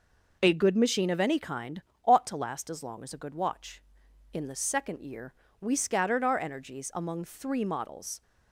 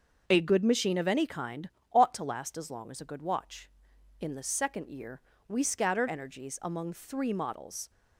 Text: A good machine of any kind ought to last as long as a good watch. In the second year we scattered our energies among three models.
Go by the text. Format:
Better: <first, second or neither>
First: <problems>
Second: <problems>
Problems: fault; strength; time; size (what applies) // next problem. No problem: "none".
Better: first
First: pauses between "kind" and "ought"; slight; at 1.8 s; 0.24 s long // pauses between "year" and "we"; slight; at 5.3 s; 0.28 s long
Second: starts louder than the rest; until 1.2 s; 6 dB // pauses between "kind" and "ought"; slight; at 1.6 s; 0.24 s long // pauses between "year" and "we"; slight; at 5.1 s; 0.28 s long // skips "our"; at 6.0 s